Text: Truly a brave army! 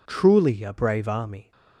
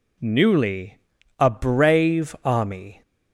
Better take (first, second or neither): first